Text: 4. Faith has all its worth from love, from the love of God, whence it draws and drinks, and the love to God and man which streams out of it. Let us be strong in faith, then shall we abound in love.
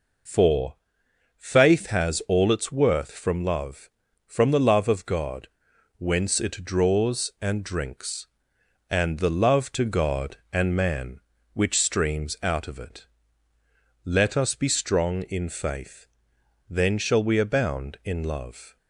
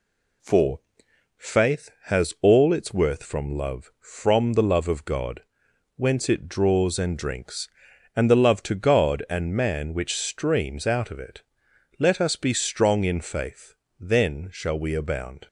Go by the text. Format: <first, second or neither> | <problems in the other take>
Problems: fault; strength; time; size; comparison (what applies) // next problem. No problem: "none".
first | stops before "in love"; at 15.4 s